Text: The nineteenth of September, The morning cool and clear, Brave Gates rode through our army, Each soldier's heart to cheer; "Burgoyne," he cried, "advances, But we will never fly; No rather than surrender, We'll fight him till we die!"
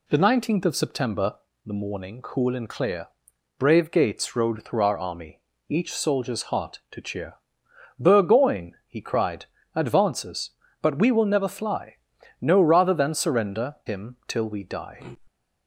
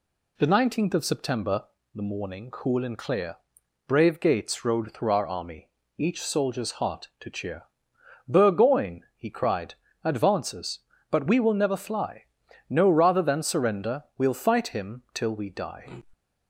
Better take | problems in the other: second | skips "We'll fight"; at 13.8 s

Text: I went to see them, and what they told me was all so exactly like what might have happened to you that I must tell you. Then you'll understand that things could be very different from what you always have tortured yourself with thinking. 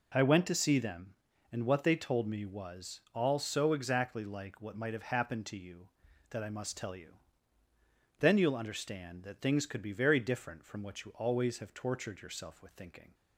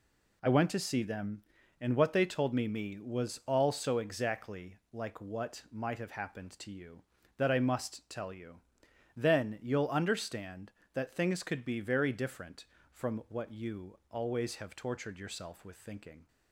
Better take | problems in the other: first | says "me" twice; at 2.6 s // pauses between "exactly" and "like"; slight; at 4.7 s; 0.16 s long

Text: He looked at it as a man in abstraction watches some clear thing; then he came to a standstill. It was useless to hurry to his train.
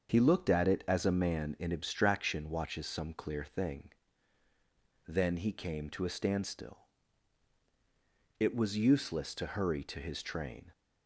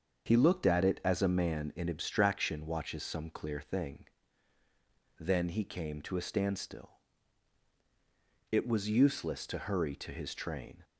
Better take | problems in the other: neither | starts louder than the rest; the same in both

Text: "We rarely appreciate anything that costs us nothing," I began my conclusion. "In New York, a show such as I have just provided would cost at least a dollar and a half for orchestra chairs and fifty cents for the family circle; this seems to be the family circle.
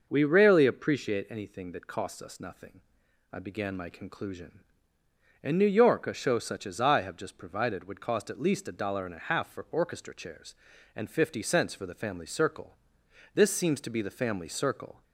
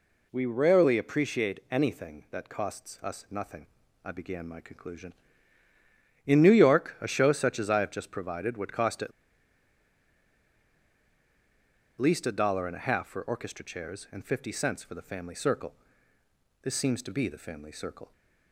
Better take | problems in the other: first | pauses between "at" and "least"; strong; at 9.1 s; 2.8 s long

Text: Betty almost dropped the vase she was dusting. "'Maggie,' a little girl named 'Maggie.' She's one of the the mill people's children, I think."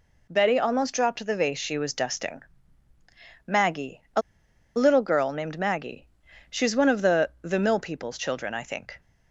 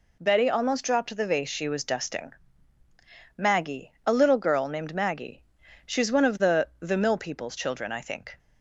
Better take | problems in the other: second | pauses between "a" and "little"; noticeable; at 4.2 s; 0.54 s long

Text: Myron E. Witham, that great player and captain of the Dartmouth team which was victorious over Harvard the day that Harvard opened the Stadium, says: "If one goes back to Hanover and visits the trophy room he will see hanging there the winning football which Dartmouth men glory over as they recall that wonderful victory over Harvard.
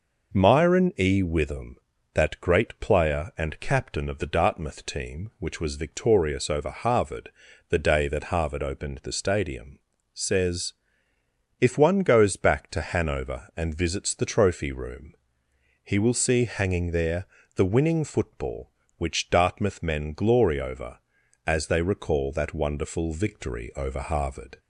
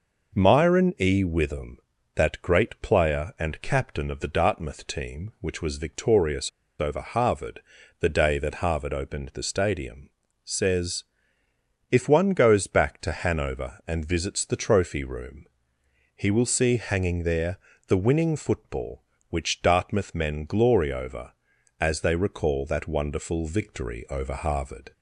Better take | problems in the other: first | pauses between "victorious" and "over"; slight; at 6.4 s; 0.29 s long // pauses between "Harvard" and "the"; at 7.6 s; 0.38 s long; also in the first // pauses between "room" and "he"; noticeable; at 15.4 s; 0.68 s long; noticeable in the first // pauses between "there" and "the"; slight; at 17.5 s; 0.32 s long; slight in the first

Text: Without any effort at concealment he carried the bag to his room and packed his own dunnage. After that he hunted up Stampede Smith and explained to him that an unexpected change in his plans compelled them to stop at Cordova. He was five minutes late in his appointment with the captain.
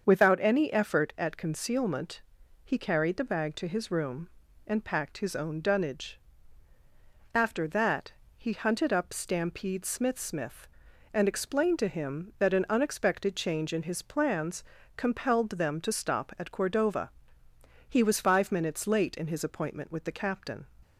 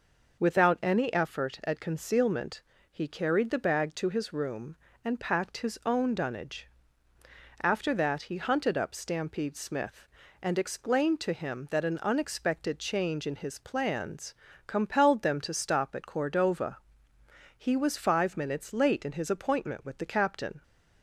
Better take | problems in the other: second | starts louder than the rest; until 1.1 s; 7 dB // pauses between "concealment" and "he"; at 2.2 s; 0.44 s long; slight in the second // pauses between "that" and "he"; slight; at 8.1 s; 0.24 s long // says "Smith" twice; at 10.1 s // pauses between "plans" and "compelled"; slight; at 14.6 s; 0.34 s long; slight in the second

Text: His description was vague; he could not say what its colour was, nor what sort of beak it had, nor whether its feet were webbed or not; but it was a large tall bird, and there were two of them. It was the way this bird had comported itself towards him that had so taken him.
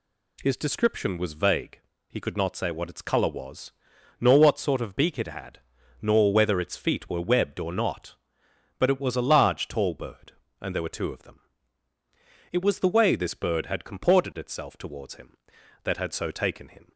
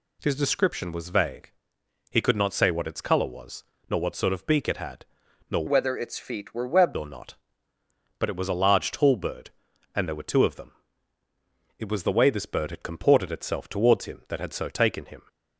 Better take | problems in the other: first | changes voice from "whether" to "webbed"; from 5.6 to 6.9 s; 1.3 s long

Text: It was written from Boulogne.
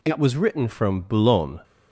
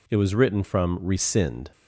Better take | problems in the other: first | says "Rescind" for "Boulogne"; at 1.0 s

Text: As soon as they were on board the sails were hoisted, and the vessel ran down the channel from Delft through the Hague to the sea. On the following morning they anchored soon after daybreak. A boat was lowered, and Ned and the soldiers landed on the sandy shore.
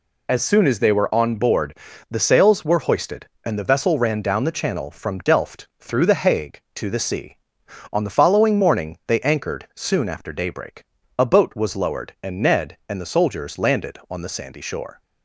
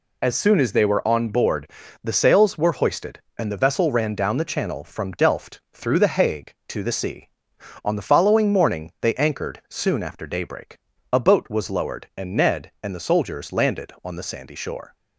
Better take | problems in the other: neither | pauses between "board" and "the"; slight; the same in both

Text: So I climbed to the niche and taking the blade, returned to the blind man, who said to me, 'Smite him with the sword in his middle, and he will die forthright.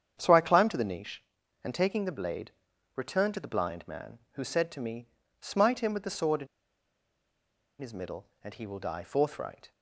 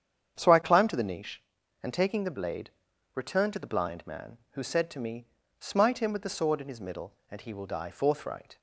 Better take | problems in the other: second | starts louder than the rest; strong; until 1.2 s; 8.5 dB; strong in the second // pauses between "in" and "his"; strong; at 6.4 s; 1.3 s long

